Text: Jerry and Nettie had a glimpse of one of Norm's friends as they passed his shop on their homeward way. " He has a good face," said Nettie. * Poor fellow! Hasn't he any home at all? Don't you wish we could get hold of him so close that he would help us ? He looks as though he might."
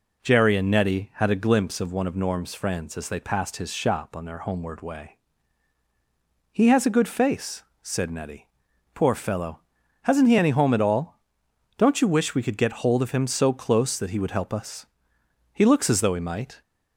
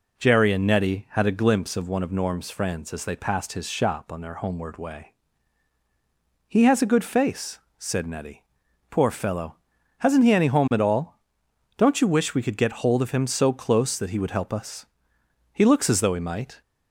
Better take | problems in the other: neither | none

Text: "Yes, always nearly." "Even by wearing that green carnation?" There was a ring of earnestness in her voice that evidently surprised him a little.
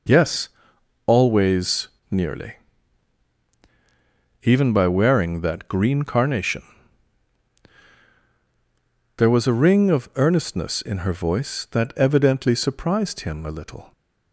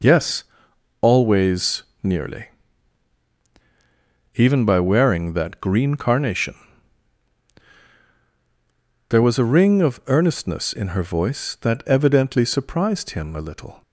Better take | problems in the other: neither | pauses between "always" and "nearly"; slight; the same in both

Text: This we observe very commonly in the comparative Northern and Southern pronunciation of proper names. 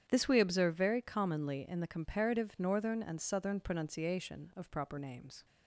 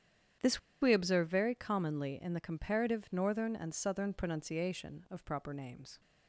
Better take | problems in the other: first | starts louder than the rest; strong; until 1.6 s; 9 dB; strong in the first // pauses between "This" and "we"; slight; at 0.5 s; 0.22 s long

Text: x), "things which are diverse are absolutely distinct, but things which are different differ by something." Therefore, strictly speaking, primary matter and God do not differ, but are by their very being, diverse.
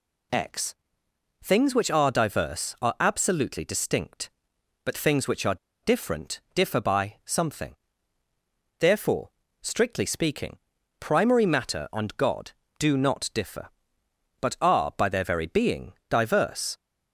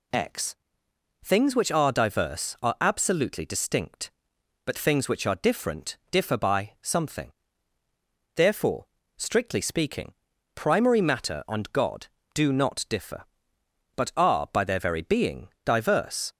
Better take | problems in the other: second | pauses between "are" and "different"; slight; at 5.5 s; 0.28 s long

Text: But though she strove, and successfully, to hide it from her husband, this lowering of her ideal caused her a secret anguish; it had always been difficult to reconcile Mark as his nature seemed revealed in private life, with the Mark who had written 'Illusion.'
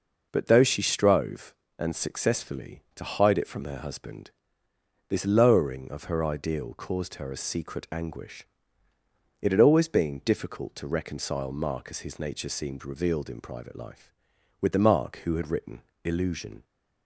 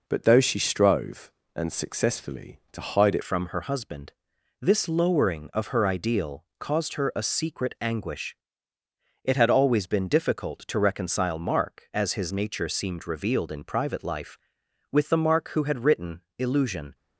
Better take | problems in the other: first | changes voice at "from"; from 3.2 s on; 13.7 s long // pauses between "written" and "Illusion"; slight; at 16.2 s; 0.18 s long; slight in the first

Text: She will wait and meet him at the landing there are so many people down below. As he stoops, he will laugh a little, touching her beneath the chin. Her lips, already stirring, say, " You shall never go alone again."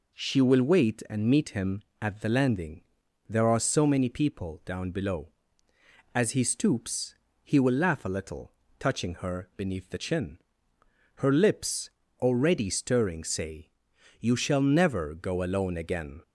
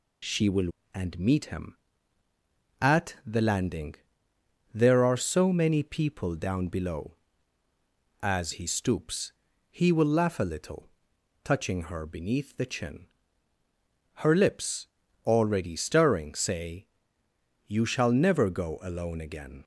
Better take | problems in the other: first | skips "wait"; at 0.8 s // pauses between "landing" and "there"; noticeable; at 3.9 s; 0.76 s long; also in the first

